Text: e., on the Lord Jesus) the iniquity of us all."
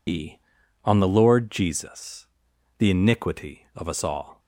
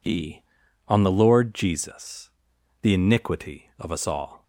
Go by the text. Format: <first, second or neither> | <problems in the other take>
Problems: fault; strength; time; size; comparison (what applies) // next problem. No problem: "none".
second | loses the start of "e"; at 0.0 s; 65 ms